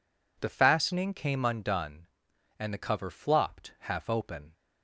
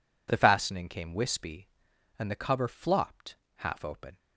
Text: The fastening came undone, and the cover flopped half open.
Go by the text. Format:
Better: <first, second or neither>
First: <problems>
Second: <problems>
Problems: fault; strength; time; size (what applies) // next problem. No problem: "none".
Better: first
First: none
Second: says "wispy" for "undone"; at 1.1 s // pauses between "flopped" and "half"; slight; at 3.3 s; 0.22 s long